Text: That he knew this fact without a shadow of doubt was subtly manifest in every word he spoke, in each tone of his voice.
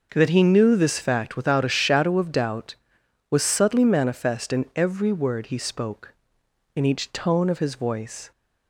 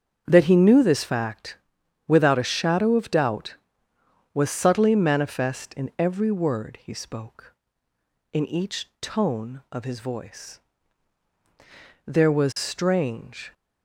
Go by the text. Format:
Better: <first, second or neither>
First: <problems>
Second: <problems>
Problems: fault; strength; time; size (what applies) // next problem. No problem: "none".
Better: first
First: none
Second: starts louder than the rest; strong; until 1.2 s; 7 dB // pauses between "fact" and "without"; noticeable; at 1.5 s; 0.50 s long // goes on to say "There was strange"; from 12.0 s on; 1.4 s long